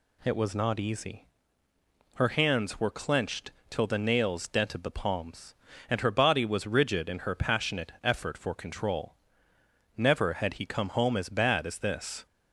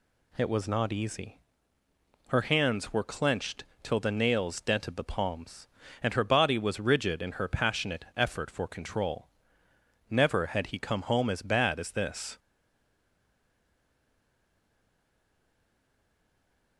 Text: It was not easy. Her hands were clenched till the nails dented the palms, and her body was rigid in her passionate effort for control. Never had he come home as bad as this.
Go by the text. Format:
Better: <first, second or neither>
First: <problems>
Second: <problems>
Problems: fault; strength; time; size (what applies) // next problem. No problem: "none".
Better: first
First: pauses between "clenched" and "till"; slight; at 3.5 s; 0.18 s long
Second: pauses between "clenched" and "till"; slight; at 3.6 s; 0.18 s long // stays silent after the last word; strong; from 12.3 s on; 4.4 s long